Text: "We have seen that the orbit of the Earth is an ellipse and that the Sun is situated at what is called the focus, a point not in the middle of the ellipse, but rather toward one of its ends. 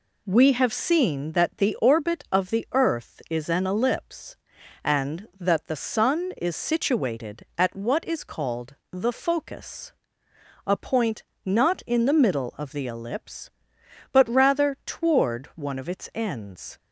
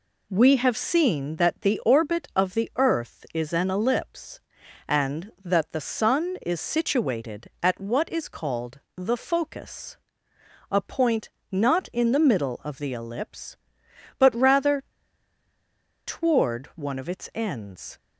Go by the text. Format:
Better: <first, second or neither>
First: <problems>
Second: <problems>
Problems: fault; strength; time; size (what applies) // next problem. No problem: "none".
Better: first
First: pauses between "called" and "the"; slight; at 8.7 s; 0.16 s long // pauses between "point" and "not"; slight; at 11.2 s; 0.20 s long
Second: pauses between "called" and "the"; slight; at 8.8 s; 0.16 s long // pauses between "point" and "not"; slight; at 11.2 s; 0.20 s long // pauses between "rather" and "toward"; at 14.8 s; 1.2 s long